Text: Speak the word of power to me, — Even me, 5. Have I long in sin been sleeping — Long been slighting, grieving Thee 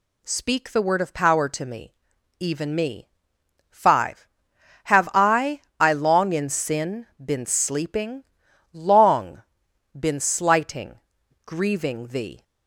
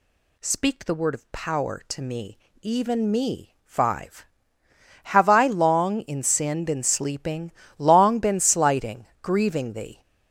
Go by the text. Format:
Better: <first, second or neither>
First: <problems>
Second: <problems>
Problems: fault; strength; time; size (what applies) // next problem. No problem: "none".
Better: second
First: says "I" twice; at 5.8 s // pauses between "sin" and "been"; slight; at 7.0 s; 0.16 s long // pauses between "Long" and "been"; noticeable; at 9.4 s; 0.52 s long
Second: none